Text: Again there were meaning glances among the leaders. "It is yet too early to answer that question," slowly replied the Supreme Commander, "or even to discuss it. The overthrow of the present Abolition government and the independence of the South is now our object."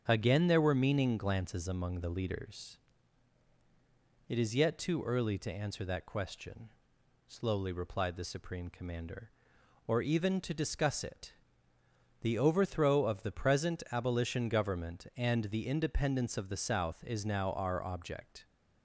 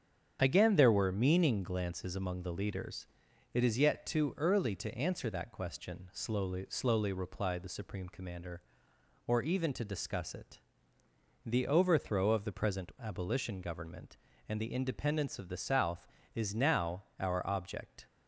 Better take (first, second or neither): first